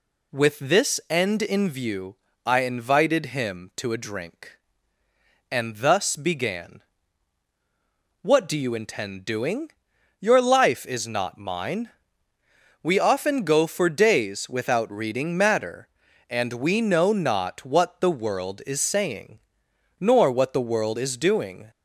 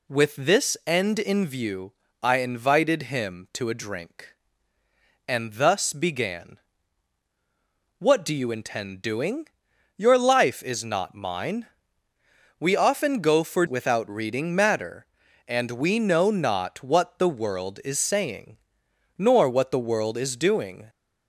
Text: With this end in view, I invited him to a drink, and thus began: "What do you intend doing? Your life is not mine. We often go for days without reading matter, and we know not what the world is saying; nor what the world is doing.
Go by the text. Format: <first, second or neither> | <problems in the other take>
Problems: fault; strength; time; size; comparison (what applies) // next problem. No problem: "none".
first | skips "days"; at 13.6 s